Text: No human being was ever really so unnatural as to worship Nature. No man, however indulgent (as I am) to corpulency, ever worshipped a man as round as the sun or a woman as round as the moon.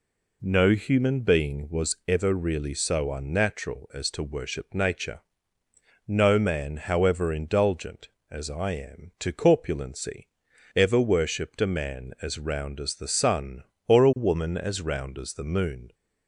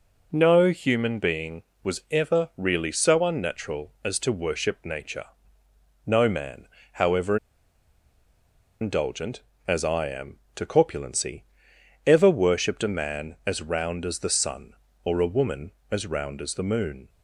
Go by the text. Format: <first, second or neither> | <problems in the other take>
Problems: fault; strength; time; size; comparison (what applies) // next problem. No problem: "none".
first | pauses between "however" and "indulgent"; strong; at 7.3 s; 1.4 s long